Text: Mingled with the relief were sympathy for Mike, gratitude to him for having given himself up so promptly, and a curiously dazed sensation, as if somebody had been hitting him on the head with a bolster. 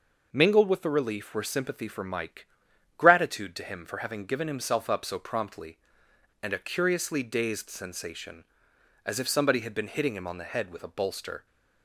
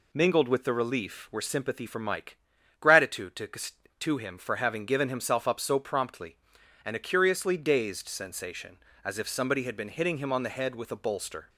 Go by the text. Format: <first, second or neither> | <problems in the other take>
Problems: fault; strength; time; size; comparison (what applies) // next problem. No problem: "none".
first | says "to" twice; at 4.0 s